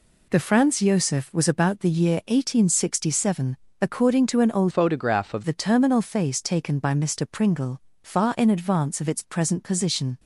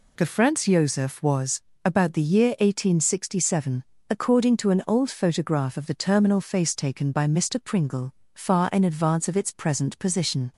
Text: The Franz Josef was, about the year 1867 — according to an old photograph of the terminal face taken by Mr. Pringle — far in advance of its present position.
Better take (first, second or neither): second